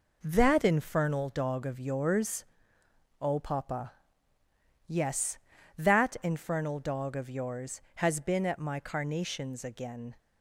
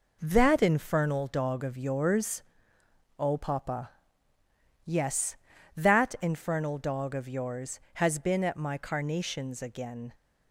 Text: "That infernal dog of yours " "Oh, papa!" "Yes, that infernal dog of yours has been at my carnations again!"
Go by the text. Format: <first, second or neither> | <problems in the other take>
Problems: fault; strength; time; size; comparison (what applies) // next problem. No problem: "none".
neither | none